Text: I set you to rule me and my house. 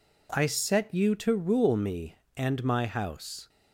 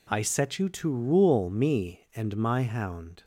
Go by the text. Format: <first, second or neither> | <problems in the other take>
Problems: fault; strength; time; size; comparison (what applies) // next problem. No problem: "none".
first | says "hound" for "house"; at 2.6 s